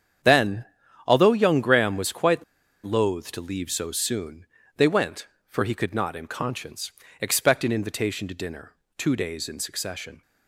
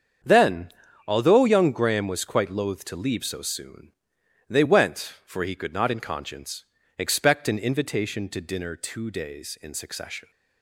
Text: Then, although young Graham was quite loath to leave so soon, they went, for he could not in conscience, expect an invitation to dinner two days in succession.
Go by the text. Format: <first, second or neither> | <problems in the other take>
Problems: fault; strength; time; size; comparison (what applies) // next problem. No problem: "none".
second | starts louder than the rest; strong; until 1.6 s; 8 dB; strong in the second // pauses between "quite" and "loath"; at 2.4 s; 0.41 s long // pauses between "dinner" and "two"; slight; at 8.7 s; 0.26 s long